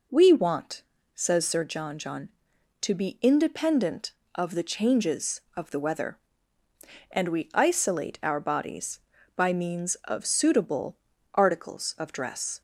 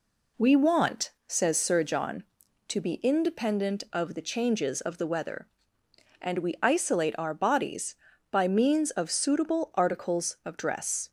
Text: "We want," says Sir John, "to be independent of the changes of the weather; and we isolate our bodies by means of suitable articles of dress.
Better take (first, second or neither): second